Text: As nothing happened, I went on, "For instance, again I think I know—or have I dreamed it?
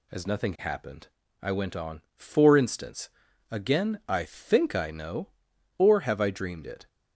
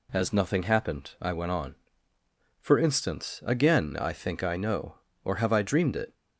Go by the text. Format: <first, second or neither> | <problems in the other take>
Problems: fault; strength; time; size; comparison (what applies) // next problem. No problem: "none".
neither | none